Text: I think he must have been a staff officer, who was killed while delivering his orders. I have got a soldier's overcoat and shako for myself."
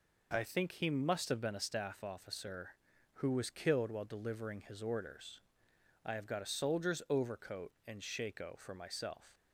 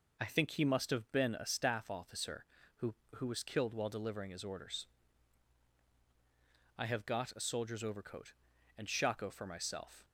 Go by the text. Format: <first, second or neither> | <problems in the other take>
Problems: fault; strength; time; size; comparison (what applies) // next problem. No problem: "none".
first | says "who" twice; at 3.1 s